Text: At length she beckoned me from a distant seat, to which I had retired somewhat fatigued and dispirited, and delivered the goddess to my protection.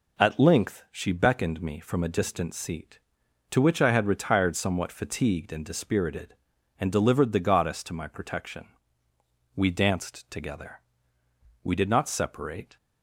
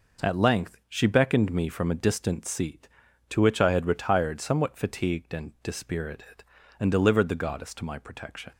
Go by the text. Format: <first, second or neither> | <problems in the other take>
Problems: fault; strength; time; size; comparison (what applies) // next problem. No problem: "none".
second | goes on to say "We danced together We did not separate"; strong; from 9.5 s on; 3.2 s long